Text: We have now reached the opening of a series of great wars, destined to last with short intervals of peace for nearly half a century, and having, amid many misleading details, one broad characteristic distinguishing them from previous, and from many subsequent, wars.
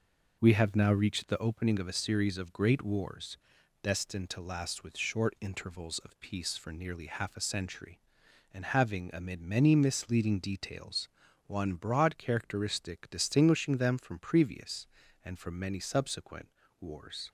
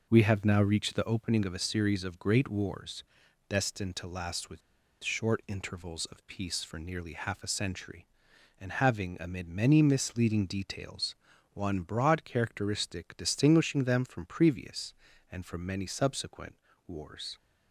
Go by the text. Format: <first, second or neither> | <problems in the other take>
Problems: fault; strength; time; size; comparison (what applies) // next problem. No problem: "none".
first | pauses between "with" and "short"; at 4.6 s; 0.43 s long